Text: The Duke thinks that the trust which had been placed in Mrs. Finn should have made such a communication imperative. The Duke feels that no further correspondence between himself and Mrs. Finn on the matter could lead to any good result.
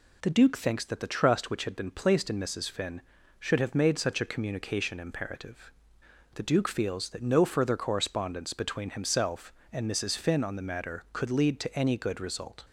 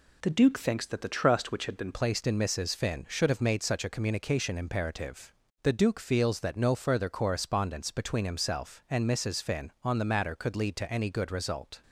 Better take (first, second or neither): first